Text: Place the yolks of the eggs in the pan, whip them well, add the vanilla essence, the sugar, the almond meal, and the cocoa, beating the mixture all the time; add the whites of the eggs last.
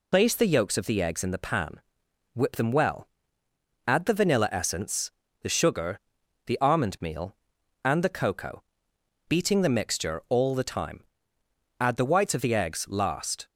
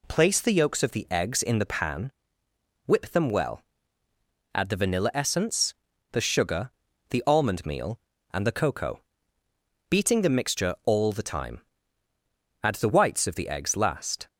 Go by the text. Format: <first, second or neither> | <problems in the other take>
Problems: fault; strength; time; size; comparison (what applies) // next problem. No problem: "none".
second | loses the start of "Place"; at 0.1 s; 65 ms